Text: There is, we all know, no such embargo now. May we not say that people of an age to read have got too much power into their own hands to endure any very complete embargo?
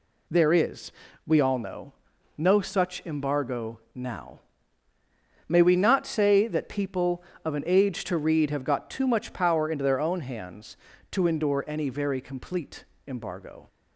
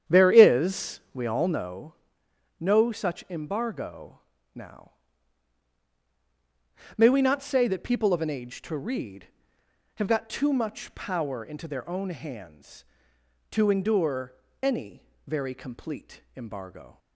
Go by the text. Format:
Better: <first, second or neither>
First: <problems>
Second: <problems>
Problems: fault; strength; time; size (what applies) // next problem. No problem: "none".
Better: first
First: pauses between "embargo" and "now"; slight; at 3.7 s; 0.16 s long // pauses between "complete" and "embargo"; slight; at 12.8 s; 0.22 s long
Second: starts louder than the rest; strong; until 1.8 s; 9 dB // pauses between "embargo" and "now"; slight; at 4.2 s; 0.34 s long // pauses between "endure" and "any"; slight; at 14.3 s; 0.28 s long // pauses between "any" and "very"; slight; at 15.0 s; 0.24 s long // pauses between "complete" and "embargo"; slight; at 16.2 s; 0.16 s long